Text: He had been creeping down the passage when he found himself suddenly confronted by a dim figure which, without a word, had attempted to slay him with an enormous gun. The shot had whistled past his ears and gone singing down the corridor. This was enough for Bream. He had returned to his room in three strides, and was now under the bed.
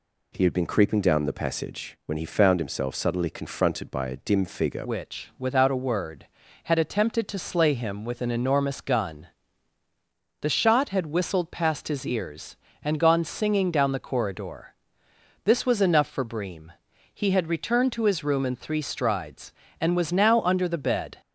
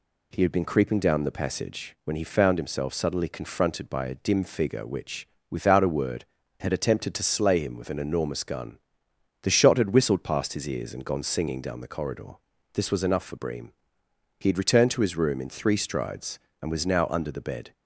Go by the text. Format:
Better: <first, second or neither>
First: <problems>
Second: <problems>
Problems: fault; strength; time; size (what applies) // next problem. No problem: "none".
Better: second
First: changes voice at "which"; from 4.8 s on; 16.4 s long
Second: none